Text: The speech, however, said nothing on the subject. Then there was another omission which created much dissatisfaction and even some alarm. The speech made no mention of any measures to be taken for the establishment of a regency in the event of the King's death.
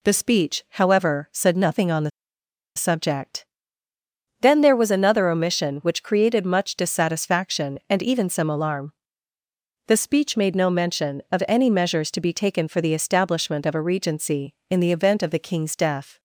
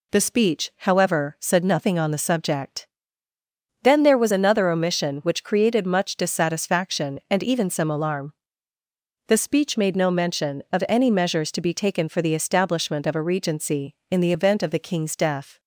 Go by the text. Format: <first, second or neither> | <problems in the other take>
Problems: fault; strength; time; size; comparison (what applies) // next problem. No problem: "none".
second | pauses between "the" and "subject"; noticeable; at 2.0 s; 0.66 s long